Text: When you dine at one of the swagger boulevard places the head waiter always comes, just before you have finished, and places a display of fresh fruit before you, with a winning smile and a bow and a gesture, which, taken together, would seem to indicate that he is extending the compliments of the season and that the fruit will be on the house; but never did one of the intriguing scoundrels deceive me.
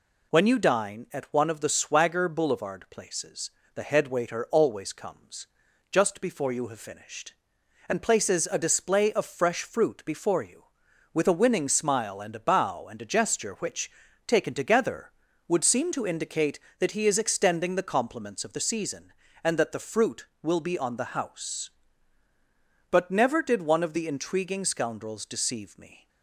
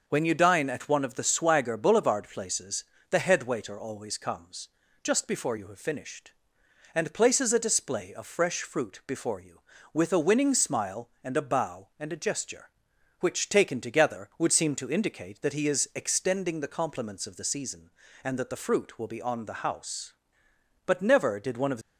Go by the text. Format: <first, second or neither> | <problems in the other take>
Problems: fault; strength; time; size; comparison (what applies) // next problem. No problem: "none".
first | pauses between "places" and "the"; slight; at 2.8 s; 0.26 s long; slight in the first // stops before "the intriguing scoundrels deceive me"; at 21.8 s